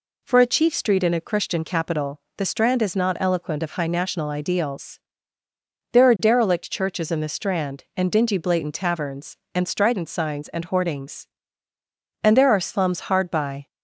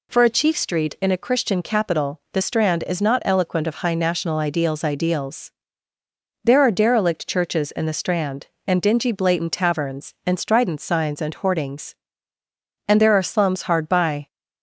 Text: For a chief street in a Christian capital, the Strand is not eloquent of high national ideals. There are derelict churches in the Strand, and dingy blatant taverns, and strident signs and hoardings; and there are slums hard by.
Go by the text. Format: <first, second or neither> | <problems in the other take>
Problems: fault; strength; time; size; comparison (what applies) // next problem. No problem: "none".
first | says "ideals" twice; at 4.8 s